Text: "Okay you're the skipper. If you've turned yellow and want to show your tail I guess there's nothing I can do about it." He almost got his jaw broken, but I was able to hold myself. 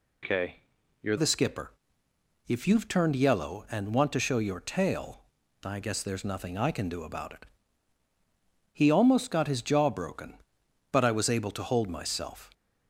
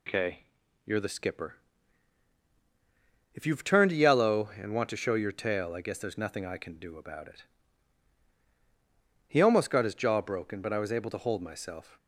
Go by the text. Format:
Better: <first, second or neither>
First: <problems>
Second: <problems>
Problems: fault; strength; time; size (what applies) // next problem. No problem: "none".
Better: second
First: pauses between "Okay" and "you're"; at 0.5 s; 0.42 s long // changes voice at "the"; from 1.1 s on; 11.4 s long // pauses between "tail" and "I"; at 5.2 s; 0.42 s long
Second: pauses between "Okay" and "you're"; at 0.4 s; 0.42 s long